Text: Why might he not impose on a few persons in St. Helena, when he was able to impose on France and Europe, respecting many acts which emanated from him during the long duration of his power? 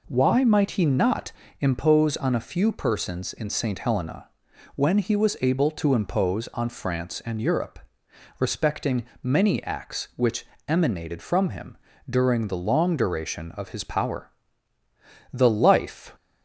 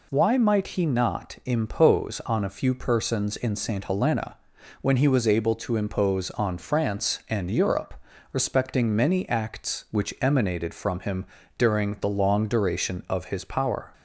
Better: second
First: pauses between "not" and "impose"; slight; at 1.3 s; 0.28 s long // pauses between "respecting" and "many"; slight; at 9.0 s; 0.18 s long // pauses between "which" and "emanated"; slight; at 10.4 s; 0.22 s long // pauses between "him" and "during"; slight; at 11.7 s; 0.32 s long // goes on to say "The life"; noticeable; from 15.3 s on; 0.82 s long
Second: pauses between "him" and "during"; slight; at 11.2 s; 0.32 s long

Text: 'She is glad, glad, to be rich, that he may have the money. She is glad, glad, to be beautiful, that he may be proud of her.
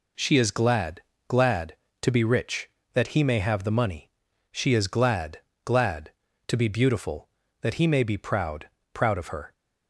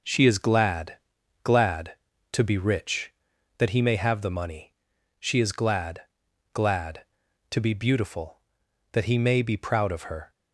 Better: second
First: says "proud" twice; at 8.9 s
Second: none

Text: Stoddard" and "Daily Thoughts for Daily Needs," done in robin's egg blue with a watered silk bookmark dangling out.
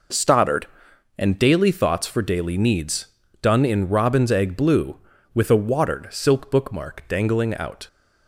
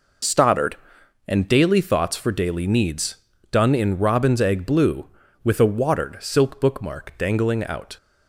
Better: first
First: none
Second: loses the start of "Stoddard"; at 0.2 s; 25 ms

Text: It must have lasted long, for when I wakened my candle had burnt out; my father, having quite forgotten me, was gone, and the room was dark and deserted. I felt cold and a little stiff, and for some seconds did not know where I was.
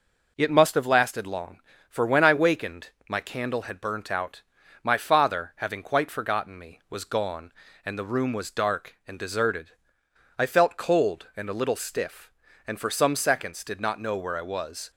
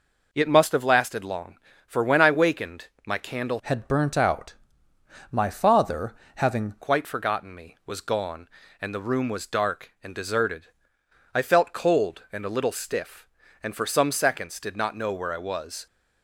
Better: first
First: pauses between "wakened" and "my"; slight; at 2.8 s; 0.18 s long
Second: pauses between "wakened" and "my"; slight; at 2.8 s; 0.18 s long // changes voice from "had" to "having"; from 3.6 to 6.7 s; 3.1 s long

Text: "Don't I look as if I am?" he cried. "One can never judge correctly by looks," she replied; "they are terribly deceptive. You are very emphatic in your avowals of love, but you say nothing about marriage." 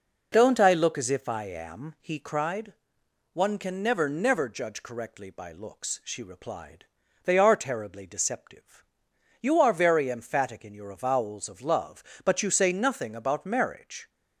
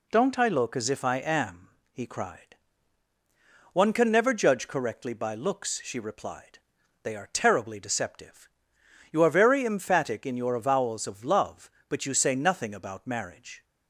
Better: second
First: says "never" twice; at 4.0 s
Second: none

